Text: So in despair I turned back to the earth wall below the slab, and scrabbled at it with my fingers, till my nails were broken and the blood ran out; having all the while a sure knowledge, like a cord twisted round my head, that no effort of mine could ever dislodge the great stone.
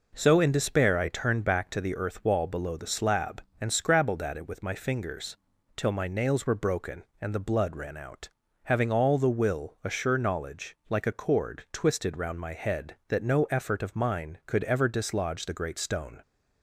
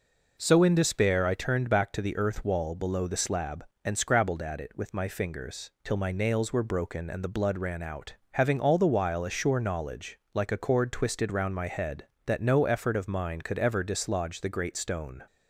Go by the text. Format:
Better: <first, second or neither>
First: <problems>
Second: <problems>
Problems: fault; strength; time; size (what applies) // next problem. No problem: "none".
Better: second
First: says "will" for "while"; at 9.2 s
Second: none